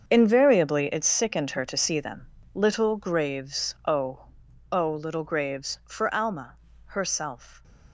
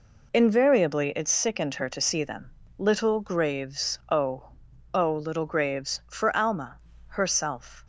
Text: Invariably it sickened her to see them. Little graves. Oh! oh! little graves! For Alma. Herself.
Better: second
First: gets quieter; strong; throughout; 13.5 dB // stays silent after the last word; slight; from 7.3 s on; 0.6 s long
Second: none

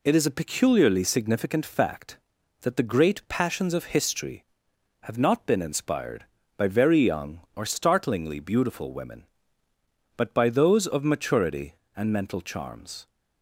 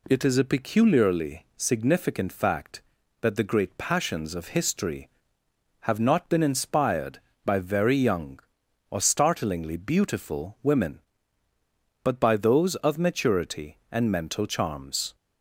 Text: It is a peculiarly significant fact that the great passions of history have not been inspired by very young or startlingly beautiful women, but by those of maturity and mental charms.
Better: neither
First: none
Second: none

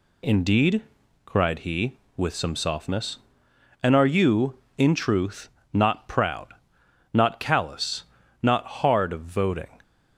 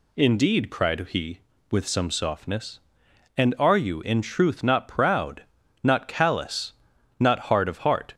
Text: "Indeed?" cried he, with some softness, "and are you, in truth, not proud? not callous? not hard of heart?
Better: second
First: says "voting" for "heart"; at 9.2 s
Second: none

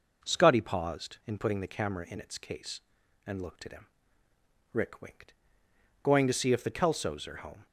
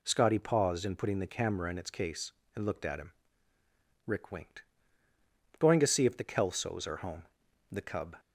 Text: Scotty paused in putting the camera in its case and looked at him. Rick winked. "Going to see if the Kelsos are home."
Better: first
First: none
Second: goes on to say "The Cub"; slight; from 7.6 s on; 0.48 s long

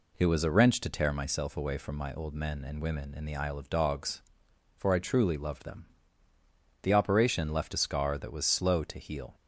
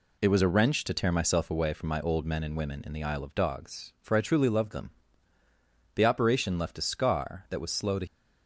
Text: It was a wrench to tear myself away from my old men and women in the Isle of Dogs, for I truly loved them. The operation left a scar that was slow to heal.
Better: first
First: none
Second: stops before "heal"; at 8.0 s

